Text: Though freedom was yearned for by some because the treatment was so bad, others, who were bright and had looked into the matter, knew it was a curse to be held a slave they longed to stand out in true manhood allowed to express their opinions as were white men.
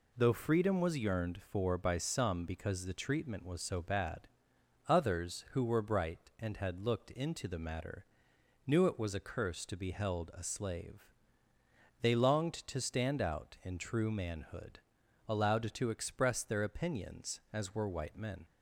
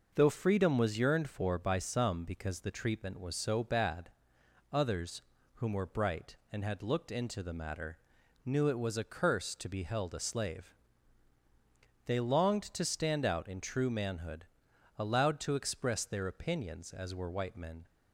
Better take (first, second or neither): first